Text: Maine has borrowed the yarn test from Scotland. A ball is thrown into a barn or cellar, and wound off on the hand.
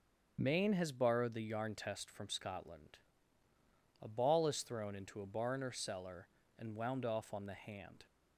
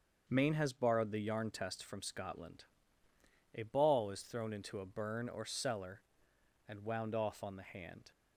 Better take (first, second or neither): first